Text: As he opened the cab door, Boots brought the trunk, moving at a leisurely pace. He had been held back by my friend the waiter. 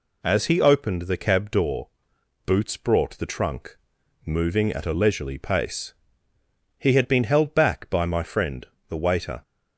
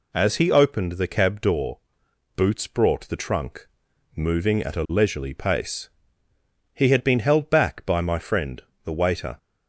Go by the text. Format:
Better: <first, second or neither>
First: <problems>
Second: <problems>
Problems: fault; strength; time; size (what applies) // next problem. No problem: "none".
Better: neither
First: pauses between "friend" and "the"; slight; at 8.6 s; 0.22 s long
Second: pauses between "friend" and "the"; slight; at 8.6 s; 0.22 s long